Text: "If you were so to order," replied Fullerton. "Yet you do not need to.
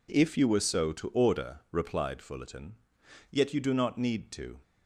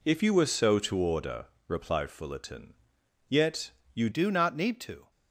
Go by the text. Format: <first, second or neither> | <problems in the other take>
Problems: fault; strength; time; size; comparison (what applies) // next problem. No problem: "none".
first | pauses between "Yet" and "you"; slight; at 3.6 s; 0.24 s long // changes voice at "do"; from 4.1 s on; 1.0 s long